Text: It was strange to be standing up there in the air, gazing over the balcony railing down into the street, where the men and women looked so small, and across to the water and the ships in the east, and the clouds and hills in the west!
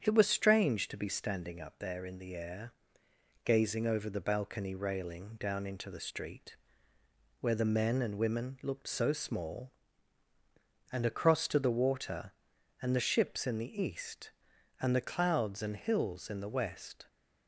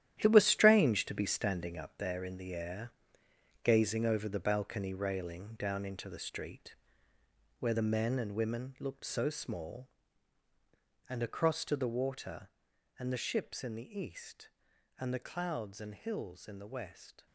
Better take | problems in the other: first | gets quieter; strong; throughout; 11 dB // starts louder than the rest; strong; until 1.2 s; 11.5 dB; strong in the first

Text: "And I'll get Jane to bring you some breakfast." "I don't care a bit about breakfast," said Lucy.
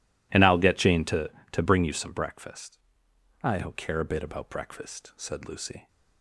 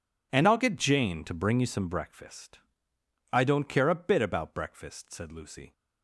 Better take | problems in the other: second | says "to" twice; at 1.5 s

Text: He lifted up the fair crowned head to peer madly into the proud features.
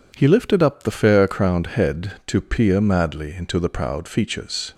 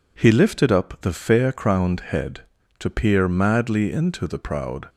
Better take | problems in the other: first | stops before "features"; at 4.8 s

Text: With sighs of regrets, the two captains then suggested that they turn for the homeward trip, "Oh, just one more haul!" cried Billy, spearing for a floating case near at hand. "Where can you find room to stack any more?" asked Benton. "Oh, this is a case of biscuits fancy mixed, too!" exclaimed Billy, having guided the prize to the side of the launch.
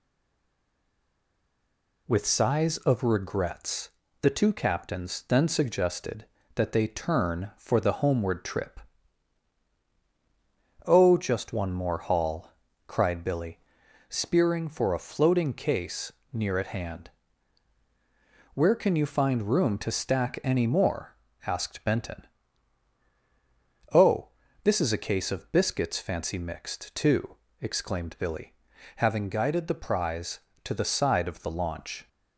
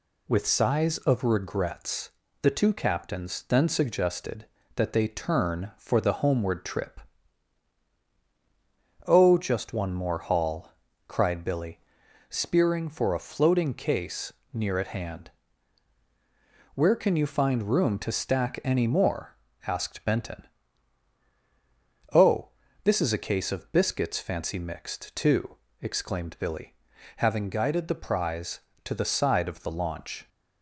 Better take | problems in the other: second | stays silent before the first word; noticeable; until 2.0 s; 2.0 s long // pauses between "case" and "near"; slight; at 16.1 s; 0.20 s long; slight in the second

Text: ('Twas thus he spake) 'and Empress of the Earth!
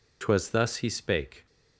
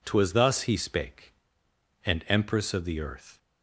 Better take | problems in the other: second | stops before "and Empress of the Earth"; at 1.4 s

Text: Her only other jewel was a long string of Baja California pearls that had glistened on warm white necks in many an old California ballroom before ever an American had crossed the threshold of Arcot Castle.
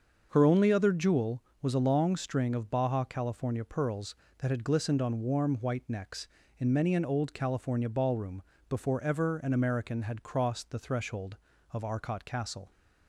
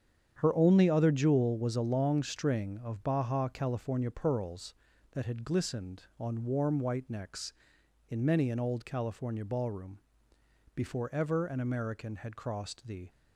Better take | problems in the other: first | starts louder than the rest; strong; until 1.3 s; 8.5 dB; also in the first // pauses between "ballroom" and "before"; noticeable; at 9.9 s; 0.78 s long; slight in the first // stops before "threshold of Arcot Castle"; at 13.0 s

